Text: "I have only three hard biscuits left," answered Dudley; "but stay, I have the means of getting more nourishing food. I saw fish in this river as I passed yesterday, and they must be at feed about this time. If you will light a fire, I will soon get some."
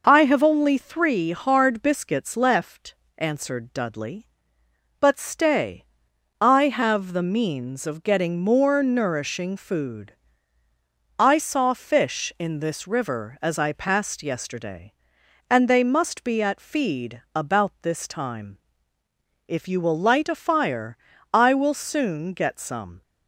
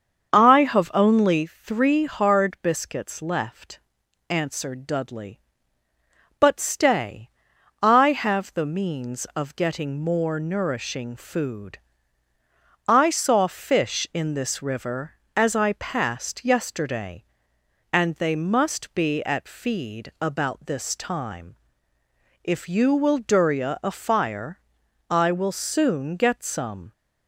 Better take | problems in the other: first | starts louder than the rest; until 1.3 s; 7 dB // says "durya" for "light"; at 23.1 s

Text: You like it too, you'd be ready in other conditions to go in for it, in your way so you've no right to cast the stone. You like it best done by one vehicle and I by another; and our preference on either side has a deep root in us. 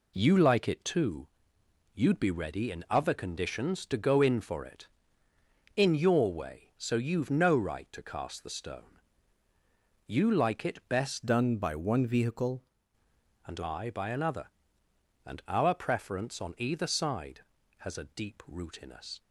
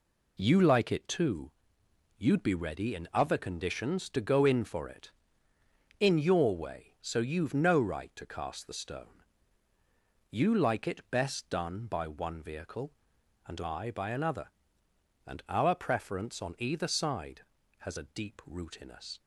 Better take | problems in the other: second | changes voice from "done" to "vehicle"; from 11.2 to 12.6 s; 1.4 s long

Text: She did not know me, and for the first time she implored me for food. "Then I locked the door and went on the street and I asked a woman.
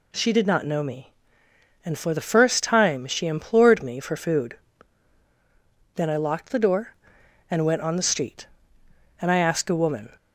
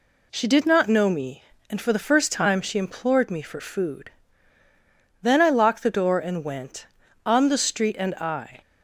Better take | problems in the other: first | stops before "asked a woman"; at 8.6 s

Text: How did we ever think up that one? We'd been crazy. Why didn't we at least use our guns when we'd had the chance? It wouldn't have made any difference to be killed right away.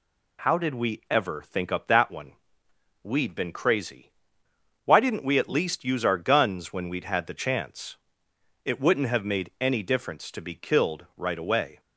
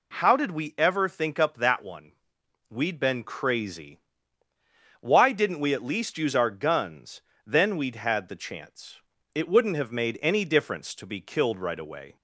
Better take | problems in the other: first | says "then" for "when"; at 7.4 s

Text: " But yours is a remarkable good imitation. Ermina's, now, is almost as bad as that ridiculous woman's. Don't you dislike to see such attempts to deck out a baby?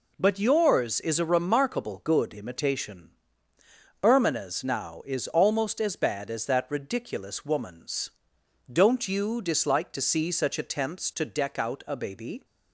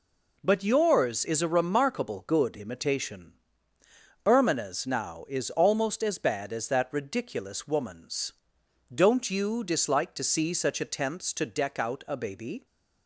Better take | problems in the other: neither | none

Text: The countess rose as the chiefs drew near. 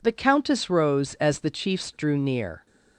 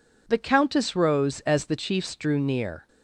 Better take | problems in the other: neither | none

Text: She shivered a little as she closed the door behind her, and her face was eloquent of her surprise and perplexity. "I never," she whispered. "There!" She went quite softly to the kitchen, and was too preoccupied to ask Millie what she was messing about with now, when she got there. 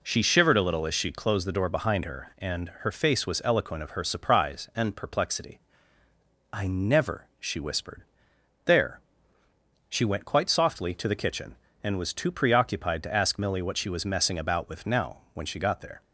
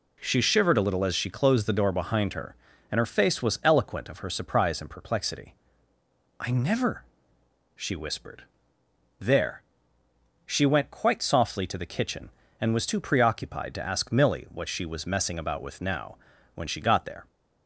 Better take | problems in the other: neither | none

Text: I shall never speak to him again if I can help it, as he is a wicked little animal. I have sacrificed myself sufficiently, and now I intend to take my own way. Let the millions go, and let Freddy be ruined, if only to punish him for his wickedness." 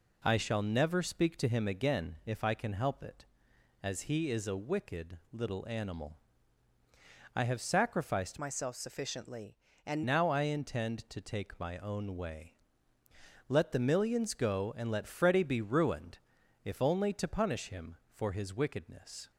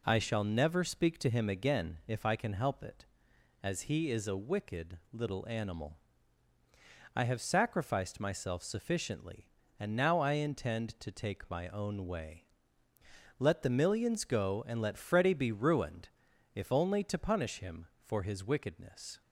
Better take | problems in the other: second | pauses between "wicked" and "little"; slight; at 5.1 s; 0.16 s long; slight in the second // changes voice from "myself" to "and"; from 8.3 to 10.0 s; 1.7 s long

